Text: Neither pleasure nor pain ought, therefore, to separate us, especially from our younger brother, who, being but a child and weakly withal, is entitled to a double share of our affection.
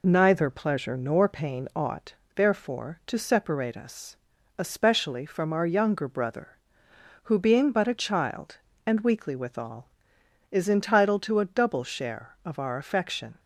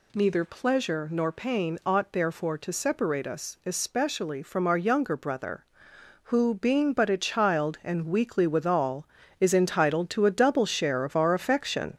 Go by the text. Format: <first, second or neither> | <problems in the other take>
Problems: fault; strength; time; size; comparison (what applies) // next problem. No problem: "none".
first | gets louder; noticeable; throughout; 4.5 dB